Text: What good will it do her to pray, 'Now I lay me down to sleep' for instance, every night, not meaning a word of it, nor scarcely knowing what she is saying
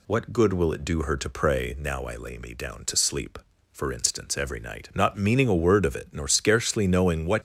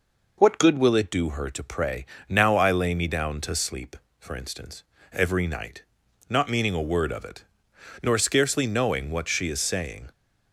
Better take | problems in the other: second | stops before "she is saying"; at 7.3 s

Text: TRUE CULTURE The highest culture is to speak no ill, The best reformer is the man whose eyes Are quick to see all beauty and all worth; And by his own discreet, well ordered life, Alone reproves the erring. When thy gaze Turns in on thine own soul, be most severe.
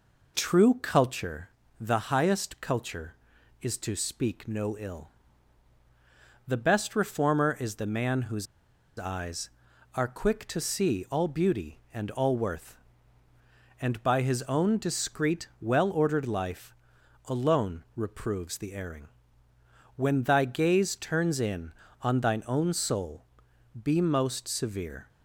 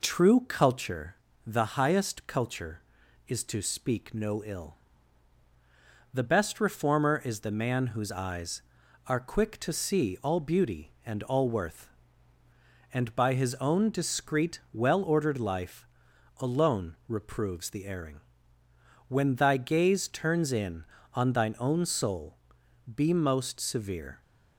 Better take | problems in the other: second | pauses between "CULTURE" and "The"; slight; at 1.4 s; 0.32 s long; slight in the second // pauses between "whose" and "eyes"; noticeable; at 8.4 s; 0.52 s long

